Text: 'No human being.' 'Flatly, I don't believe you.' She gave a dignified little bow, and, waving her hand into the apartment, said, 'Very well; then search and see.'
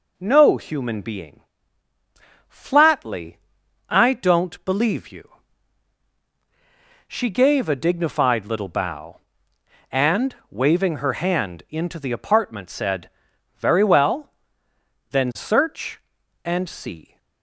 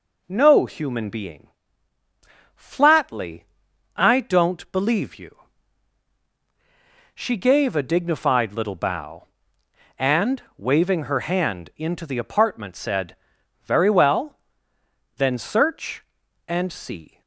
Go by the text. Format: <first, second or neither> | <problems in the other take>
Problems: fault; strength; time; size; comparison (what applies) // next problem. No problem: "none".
neither | none